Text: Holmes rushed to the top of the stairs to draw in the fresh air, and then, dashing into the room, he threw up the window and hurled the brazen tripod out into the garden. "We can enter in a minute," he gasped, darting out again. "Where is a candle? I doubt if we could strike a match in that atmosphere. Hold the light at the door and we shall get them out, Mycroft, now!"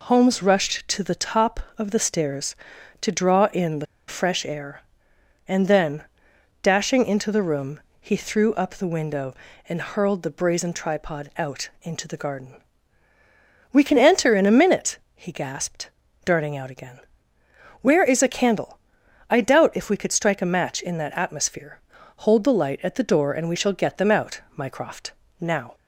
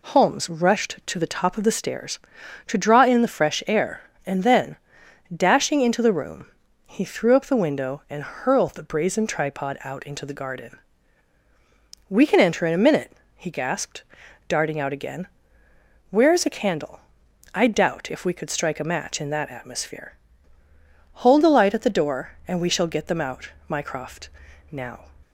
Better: second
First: pauses between "the" and "fresh"; slight; at 3.8 s; 0.22 s long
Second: none

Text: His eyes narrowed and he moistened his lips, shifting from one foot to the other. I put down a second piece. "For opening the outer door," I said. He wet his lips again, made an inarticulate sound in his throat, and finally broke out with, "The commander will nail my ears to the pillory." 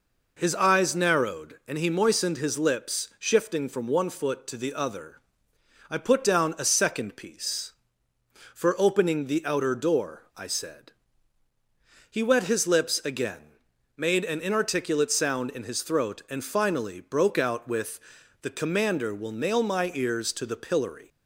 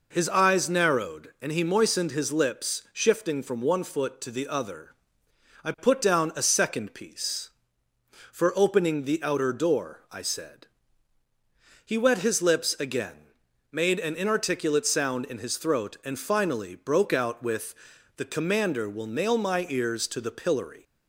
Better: neither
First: none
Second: none

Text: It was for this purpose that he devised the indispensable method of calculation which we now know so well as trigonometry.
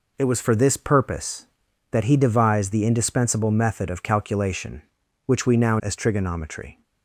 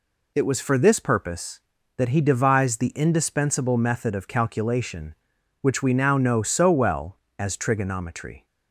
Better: second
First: skips "know so well"; at 5.7 s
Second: none

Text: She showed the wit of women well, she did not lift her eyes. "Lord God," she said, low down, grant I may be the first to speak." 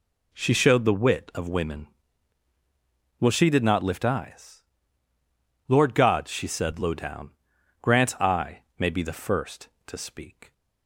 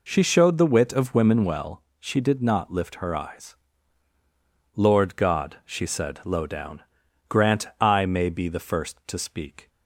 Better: second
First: pauses between "women" and "well"; strong; at 1.8 s; 1.3 s long // skips "her"; at 4.0 s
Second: none

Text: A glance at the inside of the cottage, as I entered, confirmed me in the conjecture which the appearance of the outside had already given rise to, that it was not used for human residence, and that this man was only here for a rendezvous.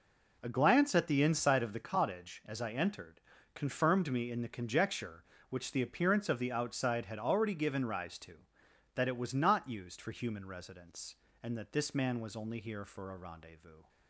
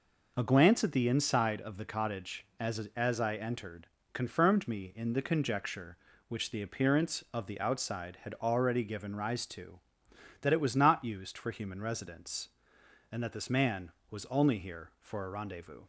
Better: first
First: none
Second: says "as" twice; at 2.9 s

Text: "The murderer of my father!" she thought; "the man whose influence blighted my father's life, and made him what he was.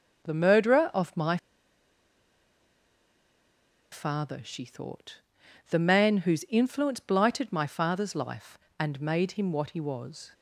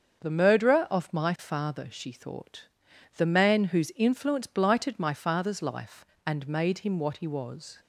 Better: second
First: starts louder than the rest; until 1.2 s; 7 dB // pauses between "my" and "father"; strong; at 1.3 s; 2.5 s long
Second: starts louder than the rest; until 1.2 s; 7 dB

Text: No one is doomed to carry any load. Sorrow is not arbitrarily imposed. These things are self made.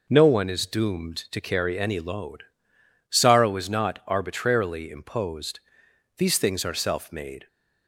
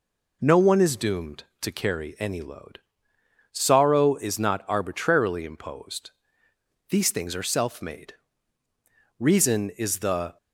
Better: first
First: none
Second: goes on to say "Reason is the"; noticeable; from 9.1 s on; 1.1 s long

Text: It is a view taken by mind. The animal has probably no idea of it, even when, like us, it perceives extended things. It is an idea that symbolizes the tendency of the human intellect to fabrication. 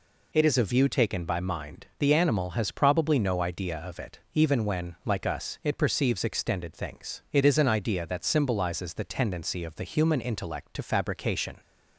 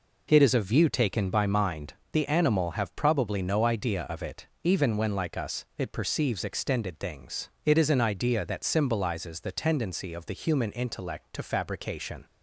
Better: first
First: none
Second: says "have" for "has"; at 2.7 s

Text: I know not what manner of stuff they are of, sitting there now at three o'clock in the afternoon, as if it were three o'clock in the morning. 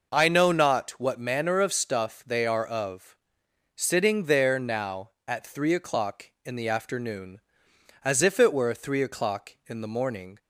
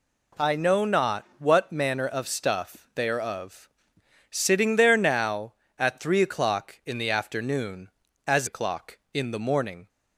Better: first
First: none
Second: skips "if it were three"; at 8.4 s

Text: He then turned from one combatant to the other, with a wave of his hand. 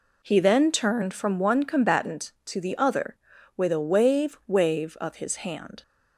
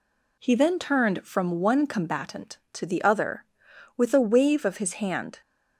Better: second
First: says "wave" twice; at 4.4 s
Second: none

